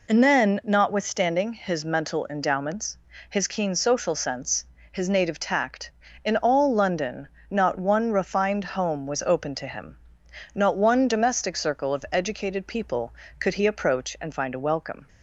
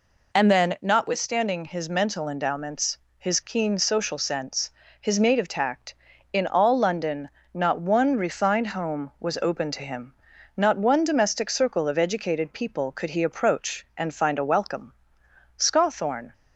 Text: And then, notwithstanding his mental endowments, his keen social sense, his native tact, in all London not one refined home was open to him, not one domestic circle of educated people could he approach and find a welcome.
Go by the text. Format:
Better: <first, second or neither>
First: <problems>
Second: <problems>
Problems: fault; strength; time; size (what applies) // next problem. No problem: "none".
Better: first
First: pauses between "London" and "not"; slight; at 7.2 s; 0.22 s long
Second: pauses between "London" and "not"; slight; at 7.2 s; 0.24 s long // goes on to say "Scawthorne"; noticeable; from 15.5 s on; 0.76 s long